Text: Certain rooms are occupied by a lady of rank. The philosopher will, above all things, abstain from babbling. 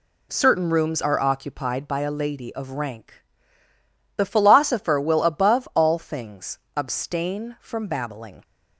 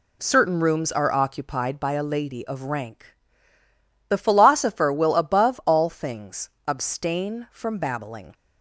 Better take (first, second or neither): neither